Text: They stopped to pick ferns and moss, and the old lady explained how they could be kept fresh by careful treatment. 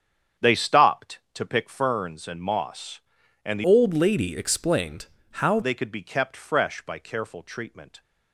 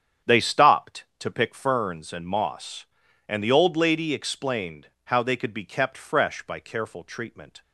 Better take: second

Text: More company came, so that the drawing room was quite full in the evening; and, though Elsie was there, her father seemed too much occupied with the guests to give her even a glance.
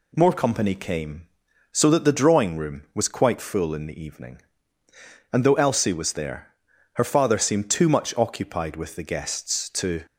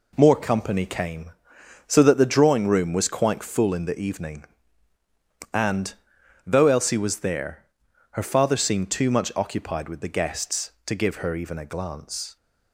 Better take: second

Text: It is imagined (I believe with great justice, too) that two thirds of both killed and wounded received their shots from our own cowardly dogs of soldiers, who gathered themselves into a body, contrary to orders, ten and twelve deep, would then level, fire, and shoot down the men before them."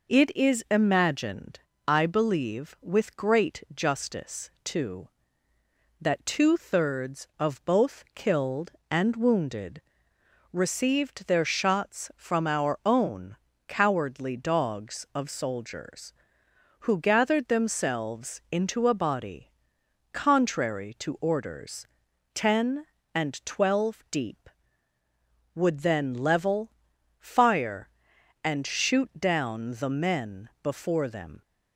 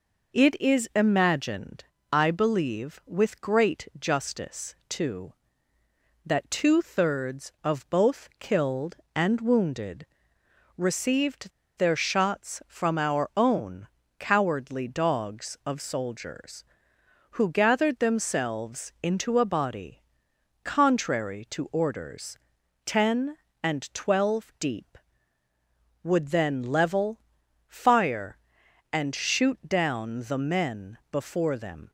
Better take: first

